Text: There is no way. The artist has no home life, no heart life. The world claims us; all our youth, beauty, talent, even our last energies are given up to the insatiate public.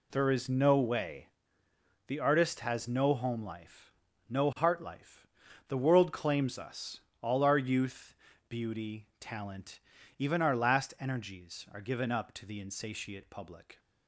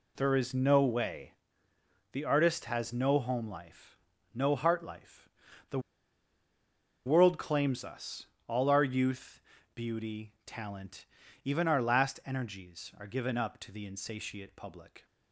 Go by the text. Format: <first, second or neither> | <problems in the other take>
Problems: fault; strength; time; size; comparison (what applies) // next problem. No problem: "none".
first | pauses between "The" and "world"; strong; at 5.7 s; 1.2 s long